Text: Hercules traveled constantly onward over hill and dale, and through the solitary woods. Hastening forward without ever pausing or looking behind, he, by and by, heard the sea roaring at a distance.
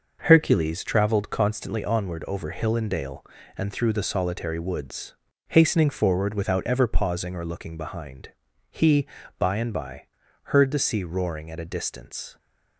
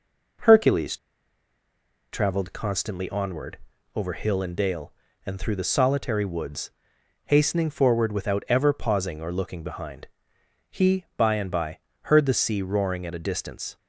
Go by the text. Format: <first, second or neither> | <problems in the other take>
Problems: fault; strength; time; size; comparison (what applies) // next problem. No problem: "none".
first | pauses between "Hercules" and "traveled"; at 0.9 s; 1.1 s long // pauses between "onward" and "over"; slight; at 3.5 s; 0.34 s long